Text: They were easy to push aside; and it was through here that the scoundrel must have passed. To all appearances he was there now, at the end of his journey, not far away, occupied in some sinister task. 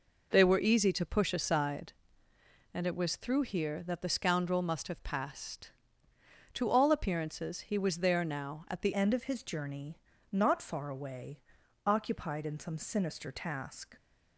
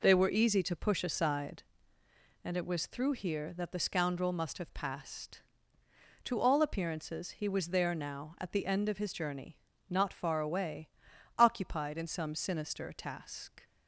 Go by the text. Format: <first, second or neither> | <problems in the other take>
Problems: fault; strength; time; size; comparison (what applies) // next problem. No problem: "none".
second | changes voice at "end"; from 8.9 s on; 5.0 s long